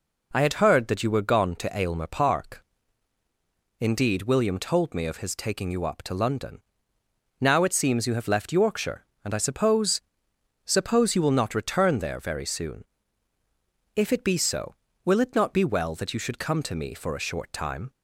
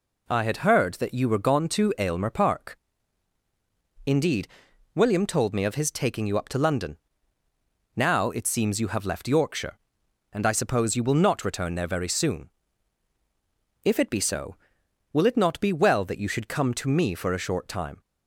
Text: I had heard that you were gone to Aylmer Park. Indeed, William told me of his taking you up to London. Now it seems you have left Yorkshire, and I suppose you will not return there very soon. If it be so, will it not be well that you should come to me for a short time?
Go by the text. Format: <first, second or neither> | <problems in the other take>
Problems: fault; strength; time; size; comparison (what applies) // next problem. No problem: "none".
second | says "suppose" twice; at 10.6 s